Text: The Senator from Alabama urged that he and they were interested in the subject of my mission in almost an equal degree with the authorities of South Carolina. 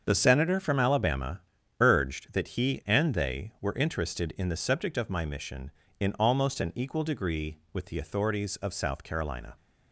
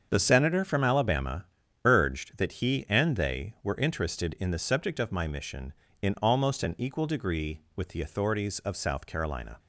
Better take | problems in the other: neither | starts louder than the rest; the same in both // pauses between "Alabama" and "urged"; the same in both

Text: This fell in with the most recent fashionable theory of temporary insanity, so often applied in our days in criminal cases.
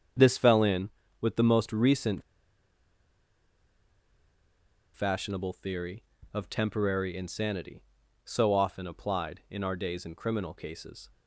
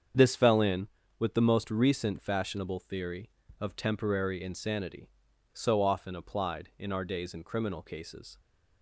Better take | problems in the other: second | starts louder than the rest; strong; until 1.5 s; 7.5 dB; strong in the second // pauses between "recent" and "fashionable"; strong; at 2.2 s; 2.7 s long

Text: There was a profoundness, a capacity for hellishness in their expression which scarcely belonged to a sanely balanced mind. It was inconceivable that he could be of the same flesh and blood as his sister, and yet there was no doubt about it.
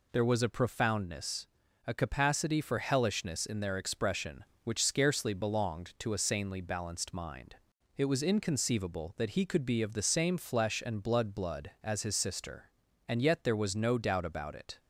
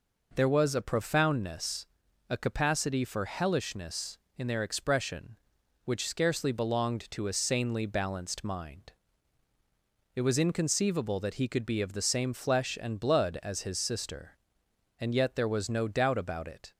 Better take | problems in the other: second | says "blood" twice; at 11.3 s

